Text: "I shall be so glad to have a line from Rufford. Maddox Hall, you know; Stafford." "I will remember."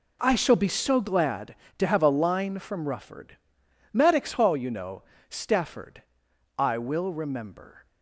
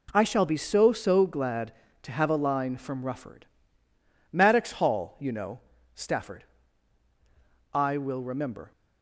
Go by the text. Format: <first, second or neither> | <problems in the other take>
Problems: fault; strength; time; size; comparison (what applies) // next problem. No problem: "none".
first | says "so" twice; at 0.9 s